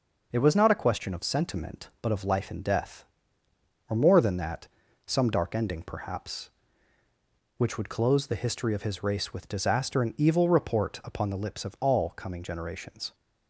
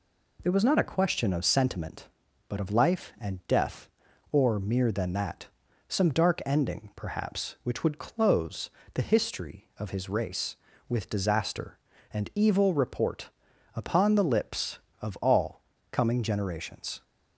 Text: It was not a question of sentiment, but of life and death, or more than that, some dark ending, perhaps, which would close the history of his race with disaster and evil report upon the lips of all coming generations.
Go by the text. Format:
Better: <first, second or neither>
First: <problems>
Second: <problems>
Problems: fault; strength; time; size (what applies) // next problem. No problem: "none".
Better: first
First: none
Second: says "mere" for "more"; at 4.5 s // pauses between "close" and "the"; slight; at 8.7 s; 0.24 s long // pauses between "report" and "upon"; noticeable; at 13.2 s; 0.46 s long // pauses between "all" and "coming"; slight; at 15.6 s; 0.30 s long